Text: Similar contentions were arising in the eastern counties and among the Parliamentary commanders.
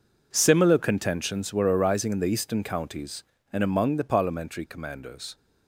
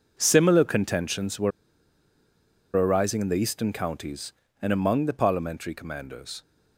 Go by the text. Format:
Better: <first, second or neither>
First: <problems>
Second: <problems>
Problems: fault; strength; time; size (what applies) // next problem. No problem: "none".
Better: first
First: none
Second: pauses between "were" and "arising"; strong; at 1.5 s; 1.2 s long